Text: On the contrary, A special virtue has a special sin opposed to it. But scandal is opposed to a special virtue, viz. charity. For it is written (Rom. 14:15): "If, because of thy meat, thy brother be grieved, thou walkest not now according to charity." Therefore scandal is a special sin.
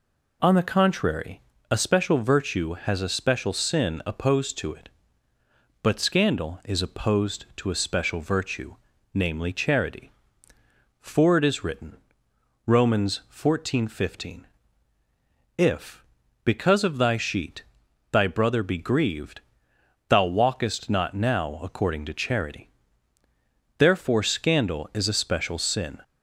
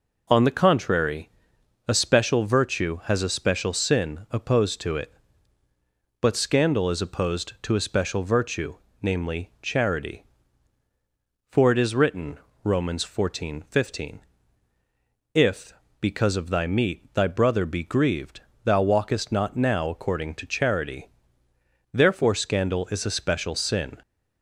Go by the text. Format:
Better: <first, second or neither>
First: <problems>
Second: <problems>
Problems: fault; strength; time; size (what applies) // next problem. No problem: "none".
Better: second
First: says "sheet" for "meat"; at 17.1 s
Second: none